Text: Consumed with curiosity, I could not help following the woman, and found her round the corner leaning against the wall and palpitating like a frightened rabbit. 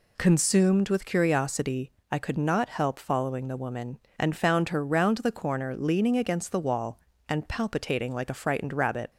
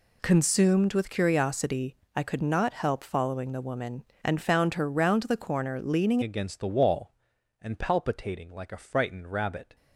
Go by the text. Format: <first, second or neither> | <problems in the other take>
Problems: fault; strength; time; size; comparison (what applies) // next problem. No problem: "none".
first | changes voice at "against"; from 6.2 s on; 3.5 s long